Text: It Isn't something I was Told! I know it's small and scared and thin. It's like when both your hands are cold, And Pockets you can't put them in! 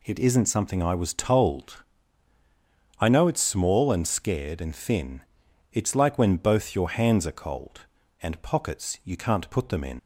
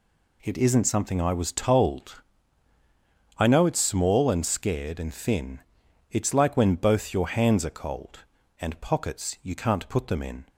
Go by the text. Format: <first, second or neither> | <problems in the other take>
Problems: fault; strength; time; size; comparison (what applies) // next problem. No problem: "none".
second | leaves "in" unfinished; at 9.9 s; 110 ms